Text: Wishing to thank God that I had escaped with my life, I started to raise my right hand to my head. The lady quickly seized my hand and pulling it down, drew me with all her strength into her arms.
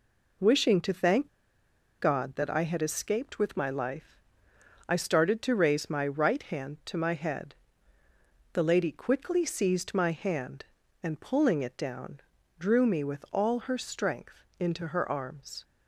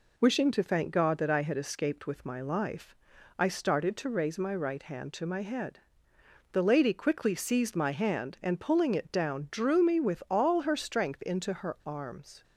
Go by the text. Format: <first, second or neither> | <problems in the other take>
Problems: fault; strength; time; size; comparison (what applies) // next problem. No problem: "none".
second | pauses between "thank" and "God"; noticeable; at 1.2 s; 0.71 s long // pauses between "strength" and "into"; slight; at 14.4 s; 0.16 s long